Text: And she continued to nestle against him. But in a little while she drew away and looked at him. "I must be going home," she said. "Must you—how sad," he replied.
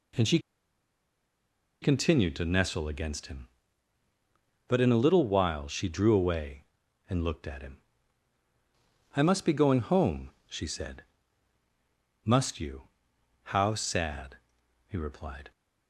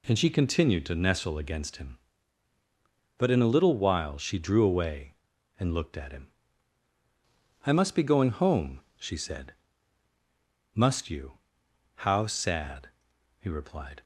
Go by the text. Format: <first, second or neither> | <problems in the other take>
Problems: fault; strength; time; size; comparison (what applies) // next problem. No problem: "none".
second | pauses between "she" and "continued"; strong; at 0.3 s; 1.4 s long